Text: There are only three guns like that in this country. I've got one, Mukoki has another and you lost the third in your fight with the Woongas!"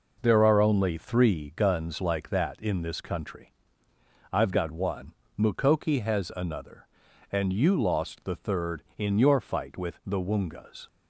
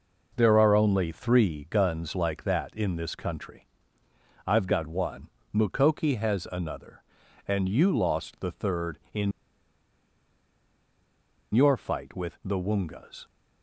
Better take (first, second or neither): first